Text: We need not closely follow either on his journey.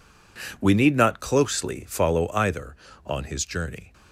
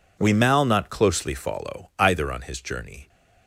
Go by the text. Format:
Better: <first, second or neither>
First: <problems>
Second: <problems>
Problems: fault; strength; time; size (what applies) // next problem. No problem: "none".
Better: first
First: none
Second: says "mal" for "need"; at 0.3 s